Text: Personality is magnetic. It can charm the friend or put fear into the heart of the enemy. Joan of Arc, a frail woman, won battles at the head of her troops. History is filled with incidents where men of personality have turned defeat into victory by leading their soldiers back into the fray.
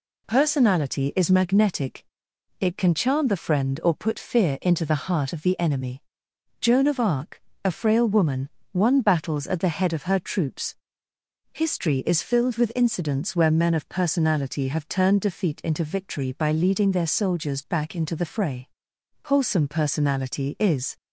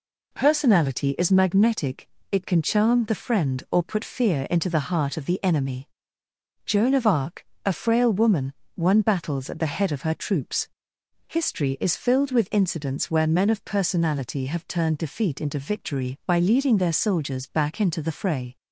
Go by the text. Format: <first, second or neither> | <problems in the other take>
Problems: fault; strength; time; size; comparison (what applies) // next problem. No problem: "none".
second | goes on to say "Wholesome personality is"; strong; from 19.2 s on; 1.7 s long